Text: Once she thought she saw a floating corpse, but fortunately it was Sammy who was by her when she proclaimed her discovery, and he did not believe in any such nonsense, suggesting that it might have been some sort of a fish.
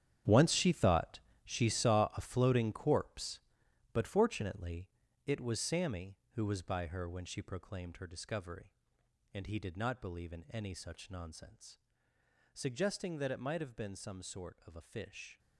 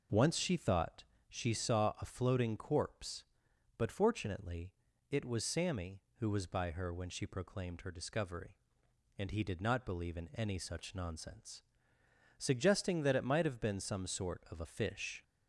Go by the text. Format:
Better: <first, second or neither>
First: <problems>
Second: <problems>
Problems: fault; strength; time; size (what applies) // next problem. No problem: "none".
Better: second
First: gets quieter; strong; throughout; 14 dB // pauses between "thought" and "she"; slight; at 1.2 s; 0.24 s long // pauses between "fortunately" and "it"; slight; at 4.8 s; 0.36 s long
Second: pauses between "thought" and "she"; slight; at 1.0 s; 0.24 s long // pauses between "fortunately" and "it"; slight; at 4.7 s; 0.36 s long